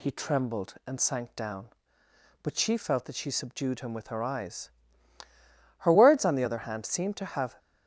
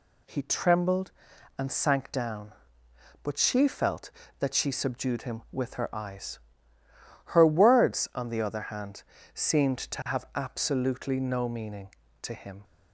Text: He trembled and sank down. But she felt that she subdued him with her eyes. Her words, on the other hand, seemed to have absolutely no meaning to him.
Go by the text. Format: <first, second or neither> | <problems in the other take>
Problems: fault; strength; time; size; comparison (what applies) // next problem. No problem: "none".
second | stops before "absolutely no meaning to him"; at 7.5 s